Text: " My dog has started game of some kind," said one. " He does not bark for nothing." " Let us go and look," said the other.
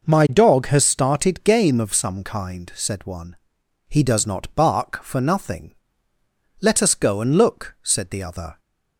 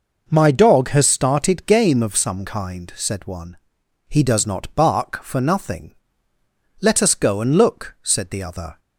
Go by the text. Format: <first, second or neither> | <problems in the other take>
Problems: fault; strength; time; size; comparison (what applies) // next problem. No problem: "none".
neither | starts louder than the rest; noticeable; the same in both